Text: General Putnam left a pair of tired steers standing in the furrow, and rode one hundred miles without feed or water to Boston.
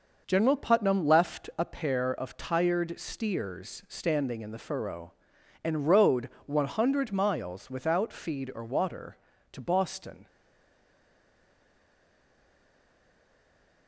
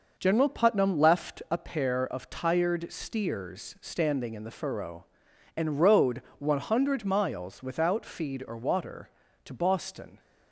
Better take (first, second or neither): second